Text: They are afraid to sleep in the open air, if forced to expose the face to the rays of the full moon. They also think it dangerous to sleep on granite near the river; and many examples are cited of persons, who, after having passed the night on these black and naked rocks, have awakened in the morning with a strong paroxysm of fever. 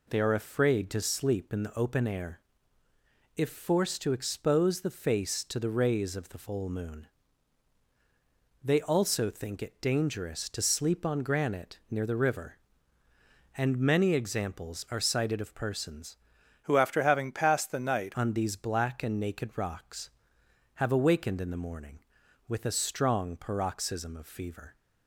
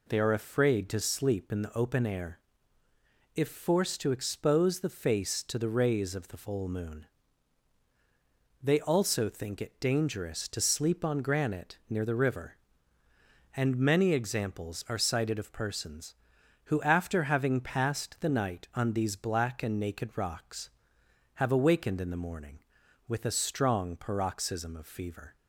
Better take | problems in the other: second | changes voice from "who" to "night"; from 16.6 to 18.1 s; 1.5 s long

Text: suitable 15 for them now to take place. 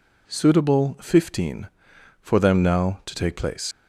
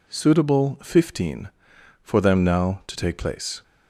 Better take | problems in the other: second | leaves "place" unfinished; at 3.7 s; 100 ms

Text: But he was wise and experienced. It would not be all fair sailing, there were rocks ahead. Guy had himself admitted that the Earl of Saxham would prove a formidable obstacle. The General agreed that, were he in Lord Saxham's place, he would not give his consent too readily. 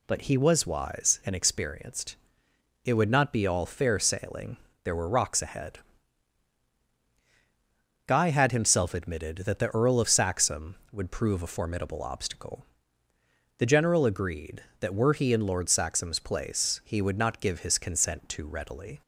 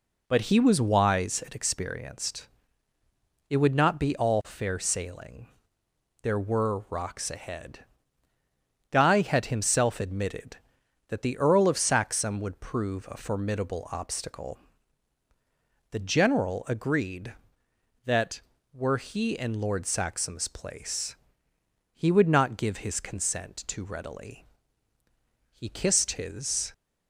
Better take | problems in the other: first | goes on to say "He kissed his"; noticeable; from 25.5 s on; 1.2 s long

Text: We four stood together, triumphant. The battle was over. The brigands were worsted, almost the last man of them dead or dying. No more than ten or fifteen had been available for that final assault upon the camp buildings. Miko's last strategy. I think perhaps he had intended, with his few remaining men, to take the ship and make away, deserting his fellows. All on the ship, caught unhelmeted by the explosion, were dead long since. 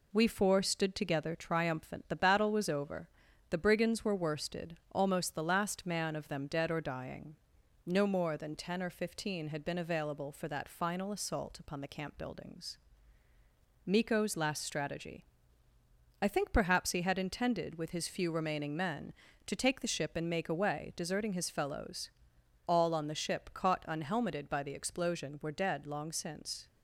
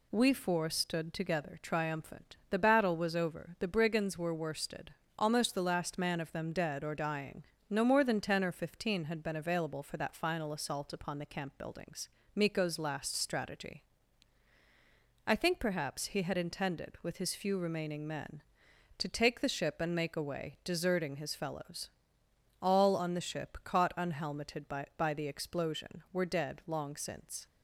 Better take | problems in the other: first | says "by" twice; at 24.9 s

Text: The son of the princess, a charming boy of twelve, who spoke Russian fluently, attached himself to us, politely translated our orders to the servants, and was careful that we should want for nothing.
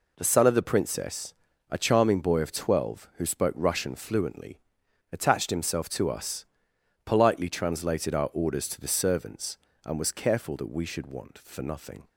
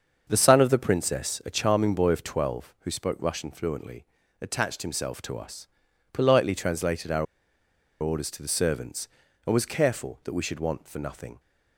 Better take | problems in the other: first | starts louder than the rest; until 1.3 s; 7 dB // pauses between "our" and "orders"; noticeable; at 7.2 s; 0.76 s long

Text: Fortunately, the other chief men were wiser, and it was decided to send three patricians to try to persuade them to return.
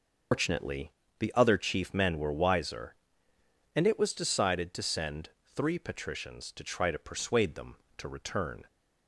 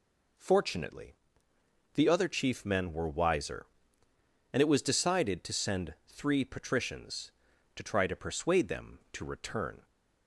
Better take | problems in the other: second | loses the start of "Fortunately"; at 0.3 s; 150 ms // pauses between "send" and "three"; slight; at 5.2 s; 0.24 s long

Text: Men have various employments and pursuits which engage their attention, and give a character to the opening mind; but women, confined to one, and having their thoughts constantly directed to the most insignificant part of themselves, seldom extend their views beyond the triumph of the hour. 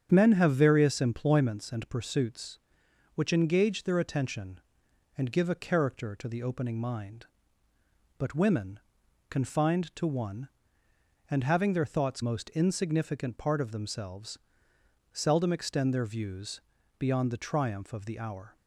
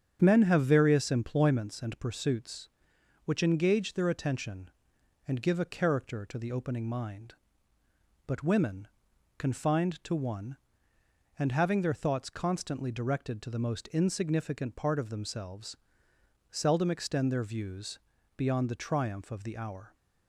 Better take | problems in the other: second | starts louder than the rest; strong; until 1.1 s; 8.5 dB; strong in the second // skips "constantly directed to the"; at 12.2 s // pauses between "views" and "beyond"; slight; at 16.6 s; 0.34 s long; slight in the second

